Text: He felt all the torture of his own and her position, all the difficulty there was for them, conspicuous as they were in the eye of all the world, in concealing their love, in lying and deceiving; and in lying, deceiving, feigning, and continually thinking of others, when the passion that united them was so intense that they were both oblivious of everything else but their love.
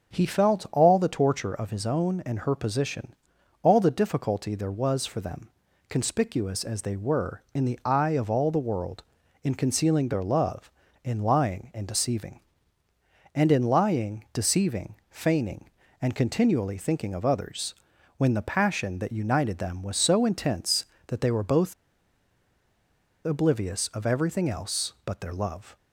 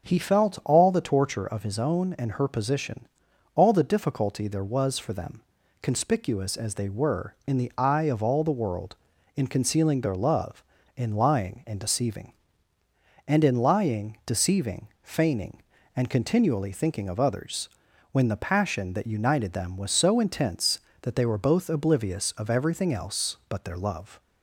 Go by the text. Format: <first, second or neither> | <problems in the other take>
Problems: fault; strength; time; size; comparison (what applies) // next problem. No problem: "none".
second | starts louder than the rest; until 1.1 s; 6.5 dB; also in the second // pauses between "both" and "oblivious"; strong; at 21.7 s; 1.5 s long